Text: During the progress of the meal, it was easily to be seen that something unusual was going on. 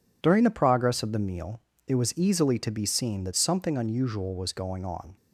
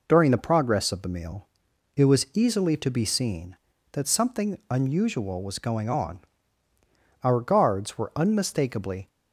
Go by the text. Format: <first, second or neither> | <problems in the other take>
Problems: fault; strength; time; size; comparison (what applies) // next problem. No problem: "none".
first | goes on to say "Our guards were unmistakably"; strong; from 7.2 s on; 1.8 s long